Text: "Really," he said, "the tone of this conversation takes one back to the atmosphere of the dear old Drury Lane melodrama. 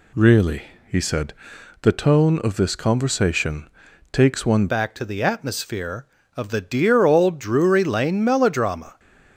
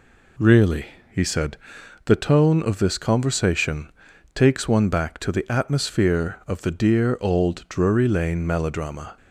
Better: second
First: pauses between "conversation" and "takes"; at 3.6 s; 0.44 s long // changes voice at "back"; from 4.6 s on; 4.3 s long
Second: pauses between "conversation" and "takes"; at 3.9 s; 0.44 s long

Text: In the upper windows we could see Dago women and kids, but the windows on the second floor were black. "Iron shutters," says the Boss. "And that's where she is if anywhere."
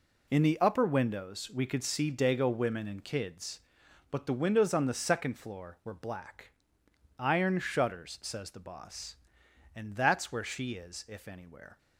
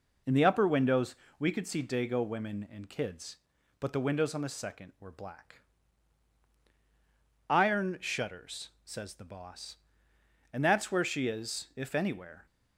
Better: first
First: none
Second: pauses between "windows" and "we"; slight; at 1.1 s; 0.22 s long // skips "floor"; at 4.9 s

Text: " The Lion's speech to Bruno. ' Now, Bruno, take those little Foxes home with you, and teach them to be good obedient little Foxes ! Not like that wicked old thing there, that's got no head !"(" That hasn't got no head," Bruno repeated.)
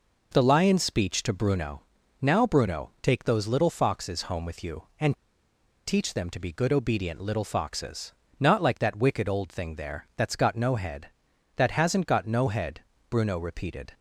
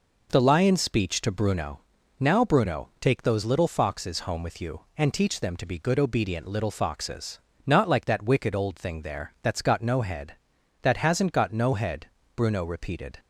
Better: second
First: pauses between "and" and "teach"; noticeable; at 5.1 s; 0.72 s long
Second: none

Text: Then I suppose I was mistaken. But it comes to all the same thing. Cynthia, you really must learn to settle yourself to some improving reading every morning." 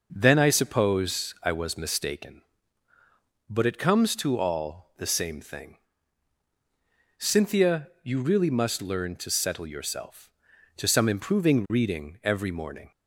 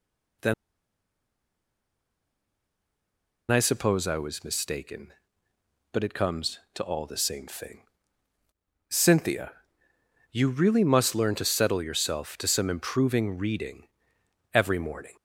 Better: first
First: none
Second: pauses between "Then" and "I"; strong; at 0.5 s; 2.9 s long // pauses between "reading" and "every"; noticeable; at 13.8 s; 0.66 s long

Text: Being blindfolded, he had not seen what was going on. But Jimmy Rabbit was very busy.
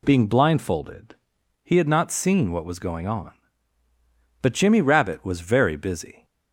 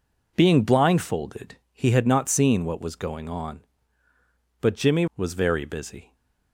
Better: first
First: none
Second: skips "Rabbit"; at 5.1 s

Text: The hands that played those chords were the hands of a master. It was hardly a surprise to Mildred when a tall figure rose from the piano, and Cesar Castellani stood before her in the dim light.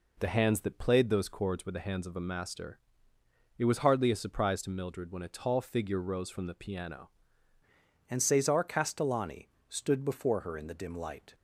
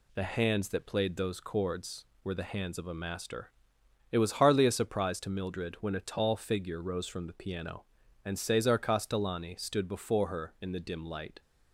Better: second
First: changes voice at "and"; from 8.0 s on; 3.3 s long // pauses between "Castellani" and "stood"; slight; at 9.4 s; 0.20 s long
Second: none

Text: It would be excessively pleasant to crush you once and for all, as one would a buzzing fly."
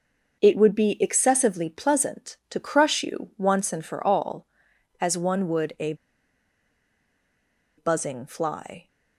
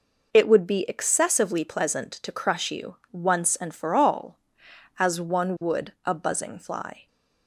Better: second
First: starts louder than the rest; noticeable; until 1.4 s; 6 dB // pauses between "a" and "buzzing"; strong; at 5.9 s; 1.8 s long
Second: none

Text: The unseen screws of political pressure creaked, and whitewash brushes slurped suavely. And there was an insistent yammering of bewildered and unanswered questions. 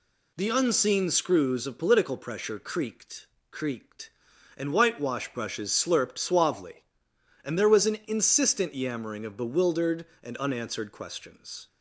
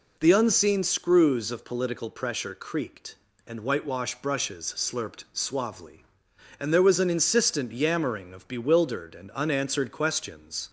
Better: second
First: says "creaked" twice; at 3.5 s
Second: none

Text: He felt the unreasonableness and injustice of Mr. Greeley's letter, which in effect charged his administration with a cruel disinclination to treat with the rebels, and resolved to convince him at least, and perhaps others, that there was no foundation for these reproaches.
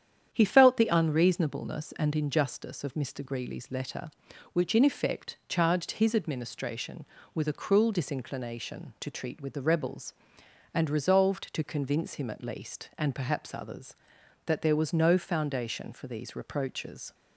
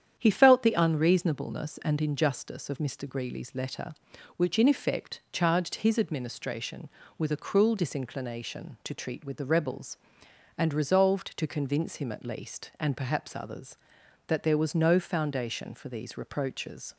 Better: neither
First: starts louder than the rest; strong; until 1.3 s; 9 dB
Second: starts louder than the rest; strong; until 1.2 s; 9 dB

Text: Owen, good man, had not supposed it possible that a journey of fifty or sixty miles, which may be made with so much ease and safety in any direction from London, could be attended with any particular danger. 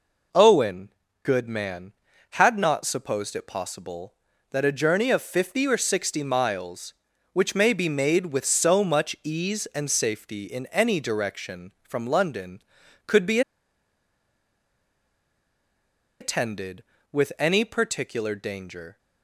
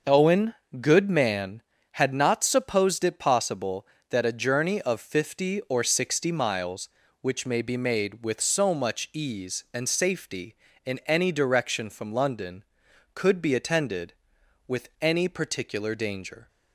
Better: second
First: pauses between "be" and "attended"; strong; at 13.4 s; 2.8 s long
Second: none

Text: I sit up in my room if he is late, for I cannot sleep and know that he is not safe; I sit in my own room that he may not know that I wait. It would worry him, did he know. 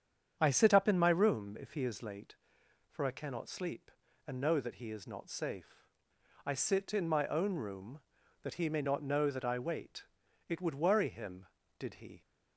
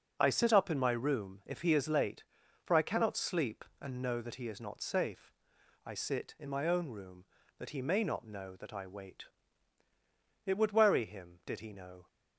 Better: second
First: starts louder than the rest; strong; until 1.4 s; 8 dB // stops before "know"; at 12.2 s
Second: none

